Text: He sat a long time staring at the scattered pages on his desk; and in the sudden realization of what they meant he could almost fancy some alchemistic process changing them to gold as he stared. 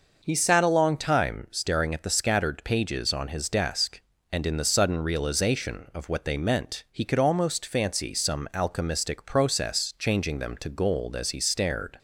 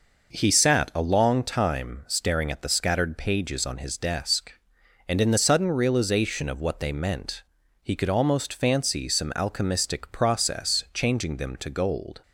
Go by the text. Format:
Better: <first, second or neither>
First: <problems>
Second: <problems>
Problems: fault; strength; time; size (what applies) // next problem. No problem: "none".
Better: first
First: none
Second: pauses between "meant" and "he"; at 7.4 s; 0.40 s long // stops before "as he stared"; at 12.2 s